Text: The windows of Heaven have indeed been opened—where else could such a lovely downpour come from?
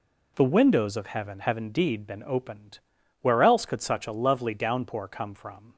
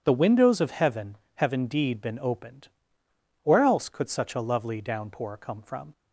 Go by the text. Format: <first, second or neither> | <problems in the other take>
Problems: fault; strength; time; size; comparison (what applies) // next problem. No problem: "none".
neither | none